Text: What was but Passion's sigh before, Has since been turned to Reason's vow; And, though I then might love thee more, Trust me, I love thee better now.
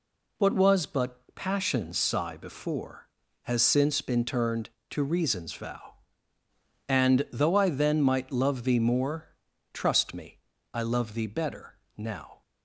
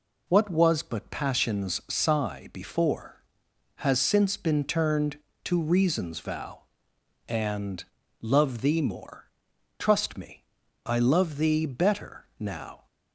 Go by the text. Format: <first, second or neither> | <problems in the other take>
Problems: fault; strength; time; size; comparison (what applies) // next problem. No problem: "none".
first | skips "though I then might"; at 8.0 s // pauses between "better" and "now"; slight; at 12.2 s; 0.16 s long; slight in the first